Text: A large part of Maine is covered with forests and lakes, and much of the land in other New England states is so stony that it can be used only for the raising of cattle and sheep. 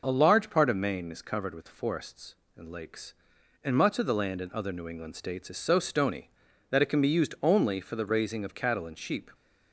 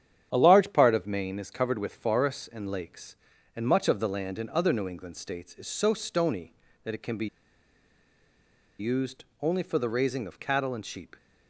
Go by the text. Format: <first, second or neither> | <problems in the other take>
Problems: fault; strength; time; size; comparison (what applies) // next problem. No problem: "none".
first | starts louder than the rest; strong; until 1.3 s; 9.5 dB // pauses between "be" and "used"; strong; at 7.2 s; 1.5 s long // pauses between "used" and "only"; slight; at 9.2 s; 0.18 s long